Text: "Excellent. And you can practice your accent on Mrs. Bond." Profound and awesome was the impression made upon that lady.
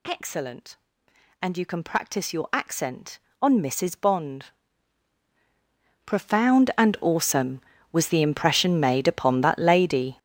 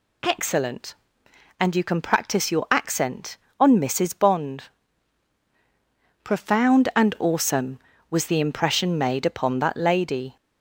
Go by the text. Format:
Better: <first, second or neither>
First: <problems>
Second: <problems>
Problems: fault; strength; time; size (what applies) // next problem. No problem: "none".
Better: second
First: gets louder; strong; throughout; 12.5 dB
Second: none